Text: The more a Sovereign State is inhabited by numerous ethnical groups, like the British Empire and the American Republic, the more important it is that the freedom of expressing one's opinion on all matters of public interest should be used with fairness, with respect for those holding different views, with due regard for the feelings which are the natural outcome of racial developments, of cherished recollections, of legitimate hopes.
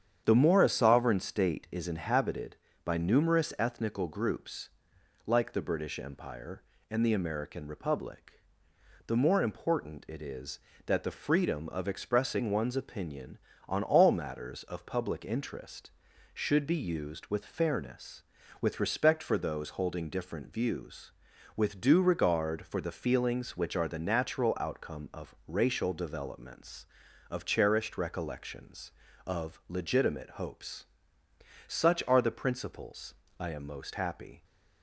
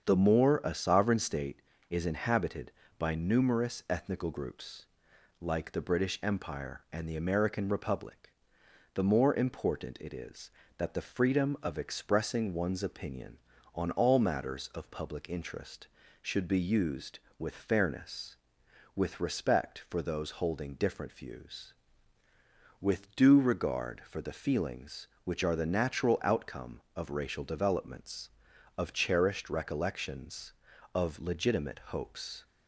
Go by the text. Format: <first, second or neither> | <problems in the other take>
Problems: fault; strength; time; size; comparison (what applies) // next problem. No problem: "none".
second | starts louder than the rest; strong; until 1.2 s; 8.5 dB; strong in the second // goes on to say "Such are the principles I am most happy"; strong; from 31.6 s on; 2.7 s long